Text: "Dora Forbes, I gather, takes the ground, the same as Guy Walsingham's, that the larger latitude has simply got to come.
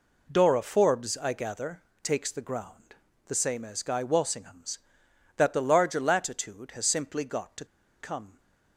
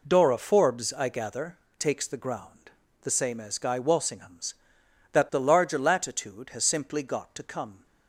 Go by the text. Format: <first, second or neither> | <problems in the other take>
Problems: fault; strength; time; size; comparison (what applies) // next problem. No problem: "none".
second | pauses between "to" and "come"; slight; at 7.6 s; 0.35 s long